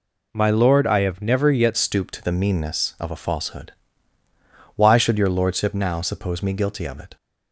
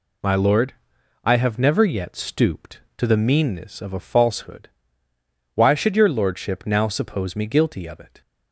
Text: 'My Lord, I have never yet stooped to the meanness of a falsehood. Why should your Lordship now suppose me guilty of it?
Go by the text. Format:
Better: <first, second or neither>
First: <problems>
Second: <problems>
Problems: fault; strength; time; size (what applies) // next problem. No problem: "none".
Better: second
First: changes voice at "stooped"; from 1.7 s on; 5.4 s long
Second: none